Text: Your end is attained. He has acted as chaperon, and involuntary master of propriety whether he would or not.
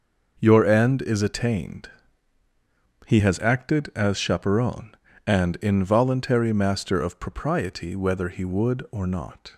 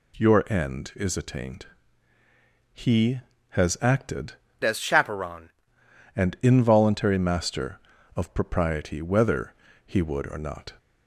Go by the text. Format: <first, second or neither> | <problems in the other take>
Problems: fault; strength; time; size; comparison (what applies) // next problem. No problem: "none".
first | changes voice from "as" to "chaperon"; from 4.6 to 5.4 s; 0.8 s long // pauses between "whether" and "he"; slight; at 9.5 s; 0.34 s long